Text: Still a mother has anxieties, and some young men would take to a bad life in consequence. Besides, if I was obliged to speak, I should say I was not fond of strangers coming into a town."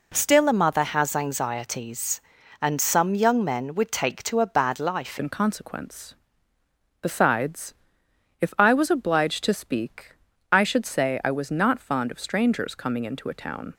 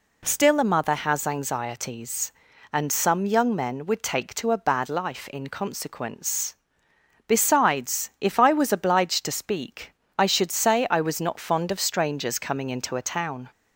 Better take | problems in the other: second | changes voice at "in"; from 5.1 s on; 8.6 s long

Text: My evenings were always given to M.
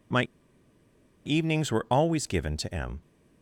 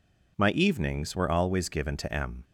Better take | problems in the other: second | pauses between "My" and "evenings"; at 0.2 s; 1.0 s long

